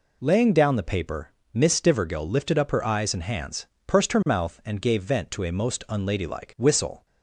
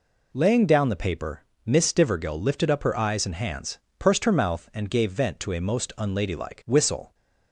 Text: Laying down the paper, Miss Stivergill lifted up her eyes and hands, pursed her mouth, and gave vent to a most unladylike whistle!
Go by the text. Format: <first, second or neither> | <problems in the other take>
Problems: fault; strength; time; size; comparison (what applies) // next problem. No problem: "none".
neither | none